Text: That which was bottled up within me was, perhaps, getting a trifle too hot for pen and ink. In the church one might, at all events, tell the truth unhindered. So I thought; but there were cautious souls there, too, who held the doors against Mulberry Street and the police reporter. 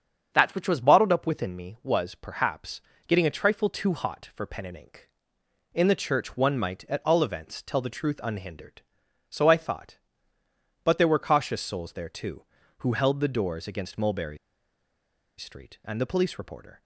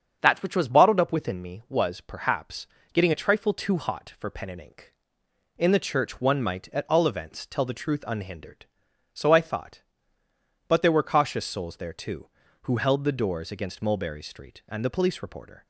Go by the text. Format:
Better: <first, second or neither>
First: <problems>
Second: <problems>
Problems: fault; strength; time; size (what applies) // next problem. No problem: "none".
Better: second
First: starts louder than the rest; strong; until 1.3 s; 7.5 dB // pauses between "Mulberry" and "Street"; at 14.3 s; 1.0 s long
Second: starts louder than the rest; strong; until 1.2 s; 7.5 dB